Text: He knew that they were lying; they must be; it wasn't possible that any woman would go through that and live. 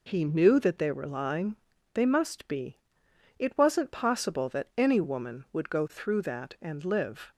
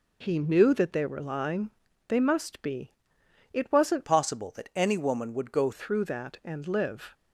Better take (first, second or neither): first